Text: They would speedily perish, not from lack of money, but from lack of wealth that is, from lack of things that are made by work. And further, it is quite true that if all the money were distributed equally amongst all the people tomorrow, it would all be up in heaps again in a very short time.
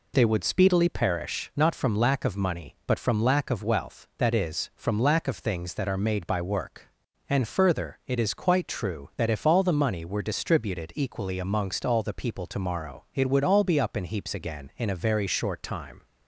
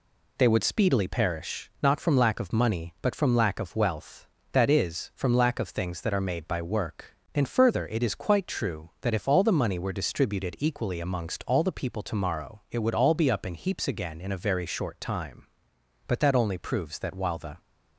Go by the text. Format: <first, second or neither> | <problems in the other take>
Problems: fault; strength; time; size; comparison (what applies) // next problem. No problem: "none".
first | goes on to say "But that only proves that while the"; from 16.0 s on; 1.5 s long